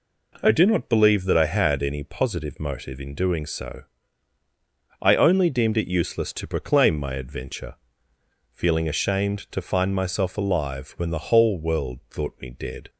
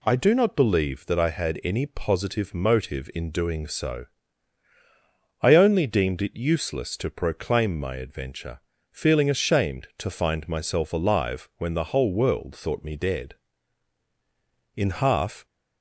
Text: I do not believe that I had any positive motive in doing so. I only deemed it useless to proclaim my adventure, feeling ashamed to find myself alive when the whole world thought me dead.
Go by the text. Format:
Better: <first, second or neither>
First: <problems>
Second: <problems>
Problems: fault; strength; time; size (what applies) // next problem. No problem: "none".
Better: first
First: none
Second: goes on to say "In half"; noticeable; from 14.7 s on; 0.70 s long